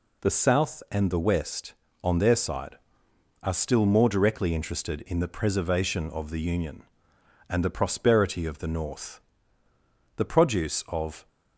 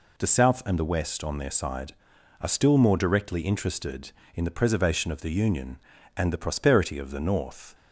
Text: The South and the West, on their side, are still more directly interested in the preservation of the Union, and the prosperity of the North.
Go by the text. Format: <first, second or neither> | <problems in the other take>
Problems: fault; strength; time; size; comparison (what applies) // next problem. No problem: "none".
second | goes on to say "The produce of"; noticeable; from 10.1 s on; 1.1 s long